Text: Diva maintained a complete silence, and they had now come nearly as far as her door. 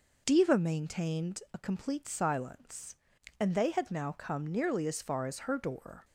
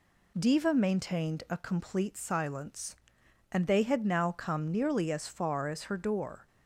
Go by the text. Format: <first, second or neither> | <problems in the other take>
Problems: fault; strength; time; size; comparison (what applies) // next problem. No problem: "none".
neither | none